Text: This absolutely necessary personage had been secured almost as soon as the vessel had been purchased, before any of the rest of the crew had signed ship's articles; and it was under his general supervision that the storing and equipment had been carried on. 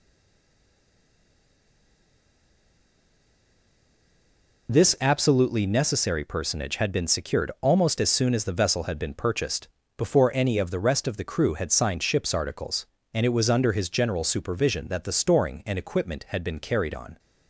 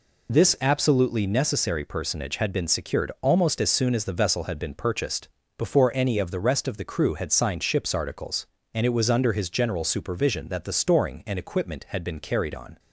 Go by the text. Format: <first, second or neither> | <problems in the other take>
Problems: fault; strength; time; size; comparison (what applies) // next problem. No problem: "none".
second | stays silent before the first word; strong; until 4.6 s; 4.6 s long